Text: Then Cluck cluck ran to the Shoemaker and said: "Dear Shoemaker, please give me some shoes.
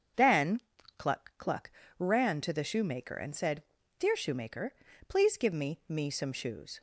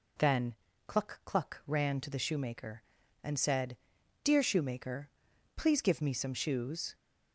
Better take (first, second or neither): second